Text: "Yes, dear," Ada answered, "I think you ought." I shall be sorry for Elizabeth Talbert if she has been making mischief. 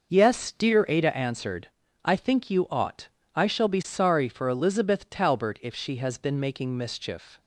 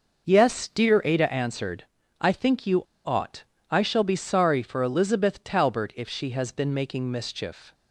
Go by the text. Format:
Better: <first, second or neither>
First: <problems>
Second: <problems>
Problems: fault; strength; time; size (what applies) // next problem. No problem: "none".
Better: first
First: none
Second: pauses between "you" and "ought"; slight; at 2.8 s; 0.23 s long